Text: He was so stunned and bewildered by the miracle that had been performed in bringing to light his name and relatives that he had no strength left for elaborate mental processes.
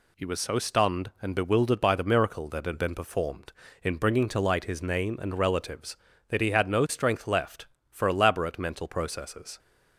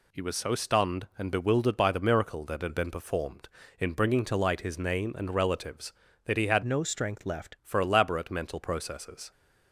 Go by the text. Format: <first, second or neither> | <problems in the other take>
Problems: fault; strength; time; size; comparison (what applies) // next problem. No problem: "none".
first | changes voice from "no" to "left"; from 6.6 to 7.5 s; 0.9 s long